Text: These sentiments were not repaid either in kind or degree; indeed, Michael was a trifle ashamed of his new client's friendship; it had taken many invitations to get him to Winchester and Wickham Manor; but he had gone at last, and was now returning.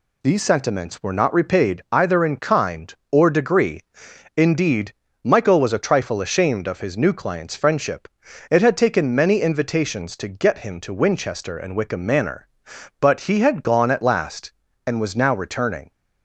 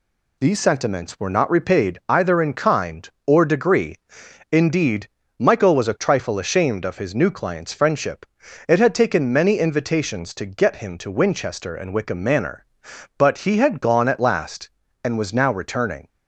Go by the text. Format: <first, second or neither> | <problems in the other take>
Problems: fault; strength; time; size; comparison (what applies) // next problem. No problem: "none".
neither | none